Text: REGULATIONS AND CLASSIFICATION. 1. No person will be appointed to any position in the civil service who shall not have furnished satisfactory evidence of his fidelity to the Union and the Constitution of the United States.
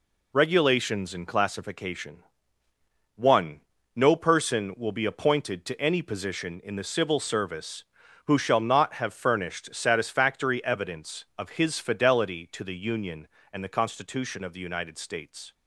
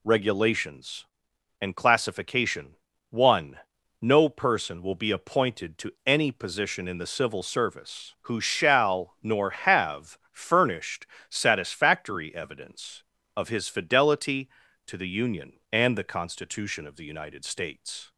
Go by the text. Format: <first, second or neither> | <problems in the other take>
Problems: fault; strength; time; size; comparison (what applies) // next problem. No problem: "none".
first | says "nor" for "not"; at 9.2 s // pauses between "have" and "furnished"; slight; at 10.1 s; 0.16 s long // pauses between "furnished" and "satisfactory"; slight; at 11.0 s; 0.24 s long